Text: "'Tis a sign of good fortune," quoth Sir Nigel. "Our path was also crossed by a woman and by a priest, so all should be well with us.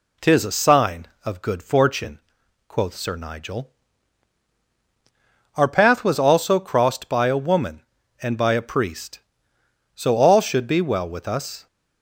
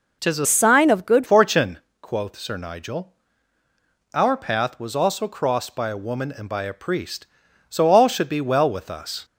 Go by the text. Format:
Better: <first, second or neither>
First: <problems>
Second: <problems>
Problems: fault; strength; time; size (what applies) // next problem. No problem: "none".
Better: first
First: none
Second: changes voice from "sign" to "good"; from 0.4 to 1.2 s; 0.8 s long